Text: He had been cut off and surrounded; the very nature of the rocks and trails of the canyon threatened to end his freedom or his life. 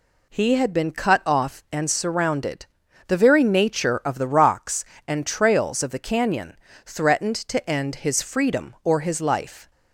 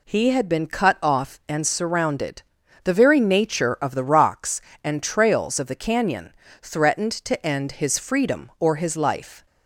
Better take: neither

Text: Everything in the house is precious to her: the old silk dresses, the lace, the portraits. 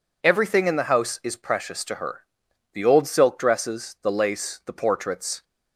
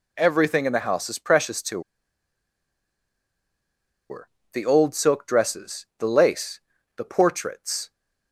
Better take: first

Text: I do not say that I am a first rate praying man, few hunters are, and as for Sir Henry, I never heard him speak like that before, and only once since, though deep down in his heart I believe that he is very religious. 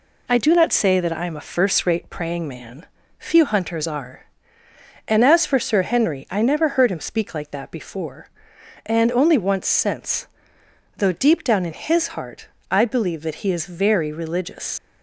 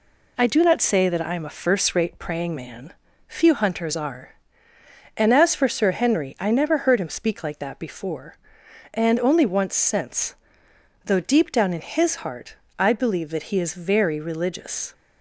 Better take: second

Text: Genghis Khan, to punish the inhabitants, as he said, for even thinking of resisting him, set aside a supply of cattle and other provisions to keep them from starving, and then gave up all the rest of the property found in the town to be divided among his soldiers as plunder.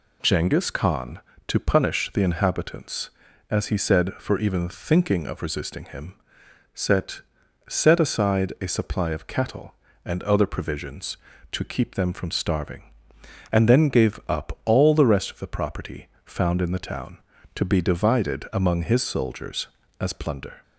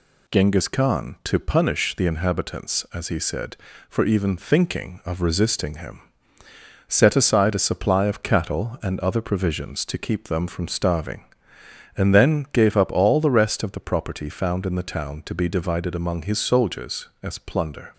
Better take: second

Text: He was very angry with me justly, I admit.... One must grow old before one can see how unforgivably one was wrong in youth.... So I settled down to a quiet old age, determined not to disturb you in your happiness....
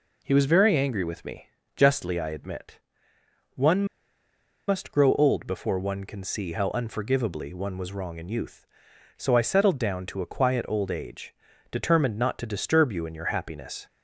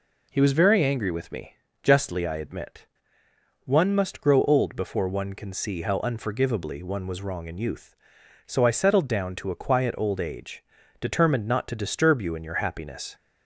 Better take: second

